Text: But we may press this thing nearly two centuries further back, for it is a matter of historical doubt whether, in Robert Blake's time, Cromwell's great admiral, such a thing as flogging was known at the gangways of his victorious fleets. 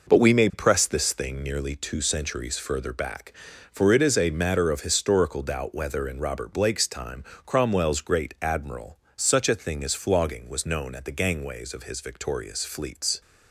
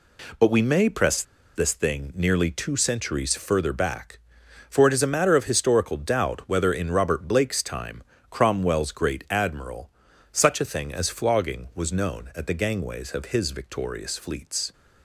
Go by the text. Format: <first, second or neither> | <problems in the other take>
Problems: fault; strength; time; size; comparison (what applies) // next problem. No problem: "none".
first | pauses between "press" and "this"; slight; at 1.2 s; 0.33 s long